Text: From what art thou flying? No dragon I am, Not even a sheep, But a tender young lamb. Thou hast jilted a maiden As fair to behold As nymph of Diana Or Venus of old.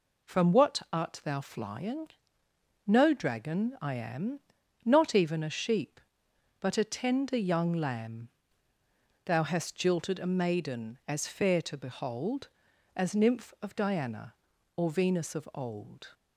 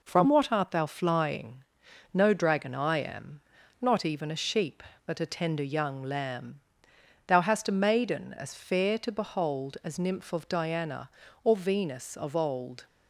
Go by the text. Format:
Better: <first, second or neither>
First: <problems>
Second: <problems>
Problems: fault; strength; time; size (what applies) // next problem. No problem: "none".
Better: first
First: none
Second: skips "jilted"; at 7.6 s